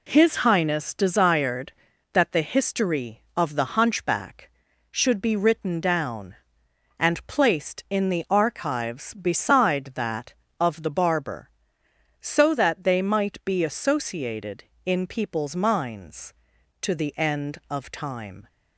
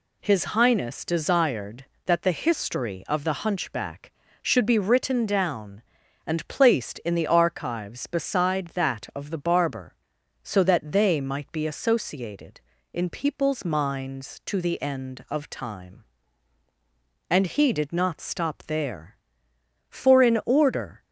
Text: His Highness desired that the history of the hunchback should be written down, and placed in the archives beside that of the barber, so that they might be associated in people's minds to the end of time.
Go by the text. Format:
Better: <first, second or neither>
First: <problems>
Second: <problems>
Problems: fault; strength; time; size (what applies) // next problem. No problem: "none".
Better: first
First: none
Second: goes on to say "And he did not stop there for in order"; strong; from 17.3 s on; 3.7 s long